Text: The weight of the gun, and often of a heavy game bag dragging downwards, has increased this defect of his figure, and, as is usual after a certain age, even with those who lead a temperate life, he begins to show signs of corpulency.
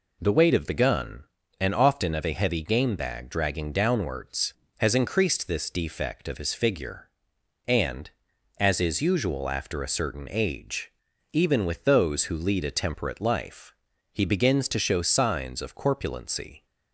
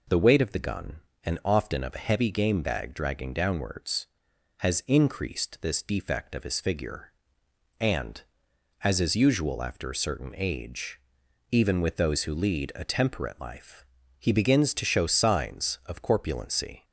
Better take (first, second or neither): neither